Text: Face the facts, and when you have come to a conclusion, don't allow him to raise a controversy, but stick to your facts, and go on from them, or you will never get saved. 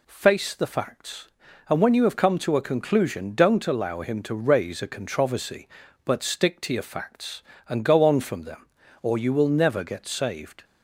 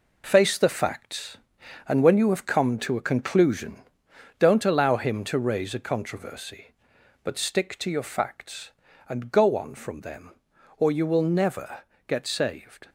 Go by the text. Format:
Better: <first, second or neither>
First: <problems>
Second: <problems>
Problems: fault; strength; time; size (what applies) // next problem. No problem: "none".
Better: first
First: none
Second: gets quieter; strong; throughout; 7.5 dB // pauses between "never" and "get"; slight; at 11.8 s; 0.26 s long